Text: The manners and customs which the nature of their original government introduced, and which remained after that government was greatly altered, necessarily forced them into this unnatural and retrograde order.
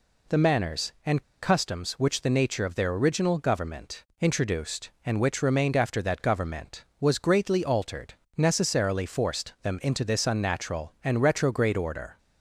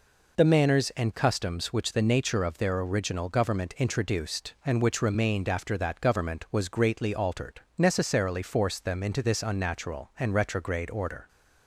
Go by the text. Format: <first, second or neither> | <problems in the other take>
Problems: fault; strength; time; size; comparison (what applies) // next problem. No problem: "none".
second | pauses between "and" and "customs"; slight; at 1.2 s; 0.18 s long // pauses between "government" and "introduced"; slight; at 4.0 s; 0.18 s long